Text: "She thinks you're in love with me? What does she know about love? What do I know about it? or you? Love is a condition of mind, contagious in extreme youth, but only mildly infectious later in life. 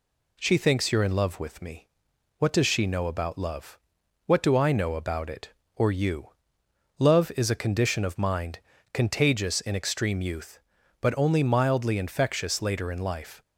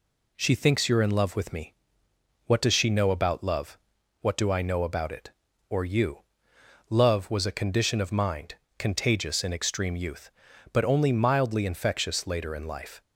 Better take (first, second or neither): first